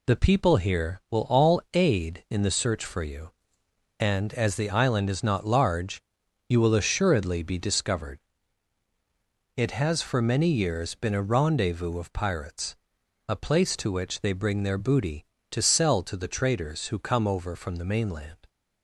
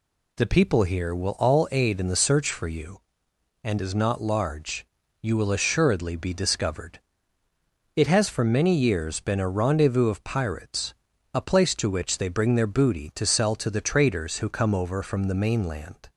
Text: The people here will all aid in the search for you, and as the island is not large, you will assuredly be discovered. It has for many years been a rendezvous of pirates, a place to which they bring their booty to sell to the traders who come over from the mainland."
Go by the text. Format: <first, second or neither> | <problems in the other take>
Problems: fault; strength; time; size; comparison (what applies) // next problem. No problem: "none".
first | skips "as the island"; at 3.7 s